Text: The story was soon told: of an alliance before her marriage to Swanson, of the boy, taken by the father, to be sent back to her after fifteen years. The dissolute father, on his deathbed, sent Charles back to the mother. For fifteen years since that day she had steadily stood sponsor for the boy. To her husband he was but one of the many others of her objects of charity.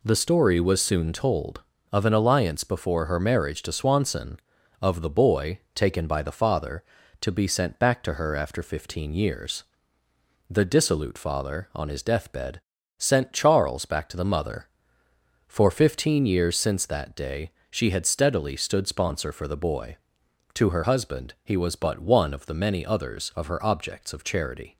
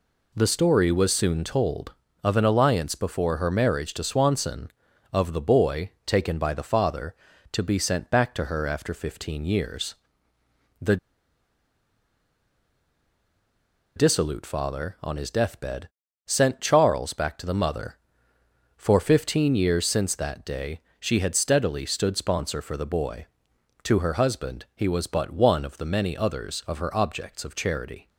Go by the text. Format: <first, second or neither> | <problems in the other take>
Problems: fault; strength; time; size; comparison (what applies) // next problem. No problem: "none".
first | pauses between "The" and "dissolute"; strong; at 10.9 s; 2.9 s long // pauses between "day" and "she"; slight; at 20.8 s; 0.18 s long; slight in the first